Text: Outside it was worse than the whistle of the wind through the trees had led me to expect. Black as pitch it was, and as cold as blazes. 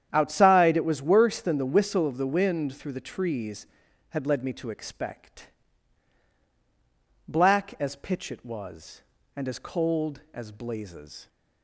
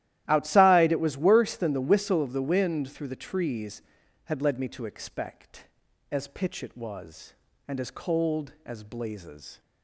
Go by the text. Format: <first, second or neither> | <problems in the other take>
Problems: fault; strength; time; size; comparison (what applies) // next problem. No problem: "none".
first | starts louder than the rest; strong; until 1.2 s; 13.5 dB; strong in the first // skips "Black"; at 5.8 s